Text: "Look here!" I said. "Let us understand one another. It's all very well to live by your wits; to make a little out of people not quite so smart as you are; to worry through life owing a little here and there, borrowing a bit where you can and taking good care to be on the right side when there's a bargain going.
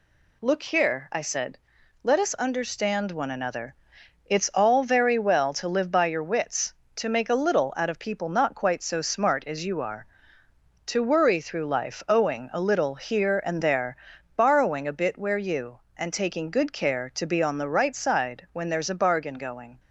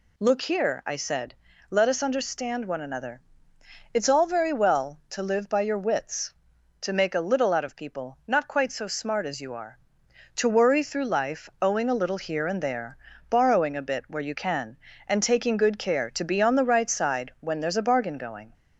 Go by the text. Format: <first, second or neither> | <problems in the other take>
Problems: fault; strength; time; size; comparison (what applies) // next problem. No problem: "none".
second | skips "can"; at 15.8 s